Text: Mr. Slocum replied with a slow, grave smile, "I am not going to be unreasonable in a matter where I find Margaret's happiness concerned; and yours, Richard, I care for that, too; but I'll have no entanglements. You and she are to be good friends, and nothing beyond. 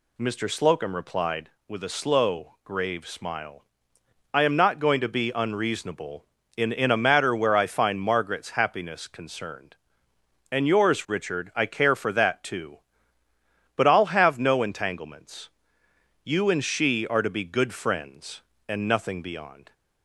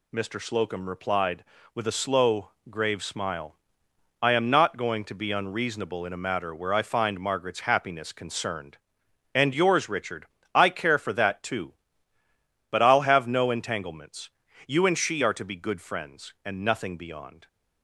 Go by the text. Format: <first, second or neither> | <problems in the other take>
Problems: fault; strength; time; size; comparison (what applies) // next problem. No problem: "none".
second | says "in" twice; at 6.6 s